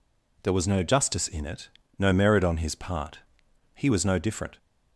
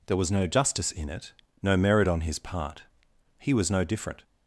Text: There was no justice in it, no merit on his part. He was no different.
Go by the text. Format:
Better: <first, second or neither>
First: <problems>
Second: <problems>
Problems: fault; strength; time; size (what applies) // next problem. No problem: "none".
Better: neither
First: none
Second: none